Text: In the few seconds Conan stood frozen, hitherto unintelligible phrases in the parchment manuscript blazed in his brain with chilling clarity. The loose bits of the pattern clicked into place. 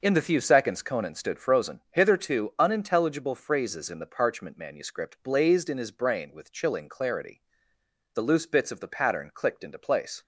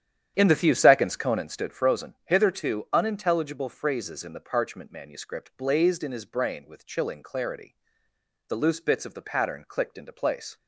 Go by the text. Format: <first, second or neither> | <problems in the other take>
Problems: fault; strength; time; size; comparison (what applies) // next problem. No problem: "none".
first | starts louder than the rest; strong; until 1.6 s; 10 dB